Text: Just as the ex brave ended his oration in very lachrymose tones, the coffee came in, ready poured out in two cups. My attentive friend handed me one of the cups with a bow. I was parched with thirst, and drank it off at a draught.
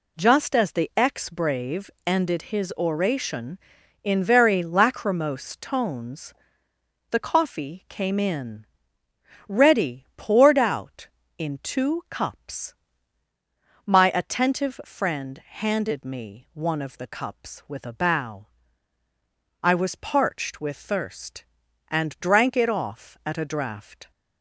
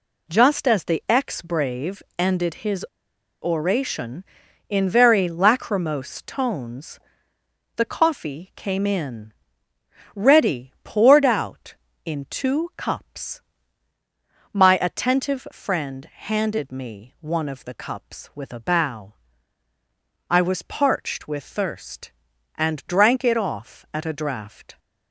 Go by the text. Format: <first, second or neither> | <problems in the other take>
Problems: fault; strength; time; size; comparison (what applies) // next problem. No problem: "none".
first | pauses between "brave" and "ended"; slight; at 2.0 s; 0.16 s long; slight in the first // pauses between "his" and "oration"; noticeable; at 2.8 s; 0.59 s long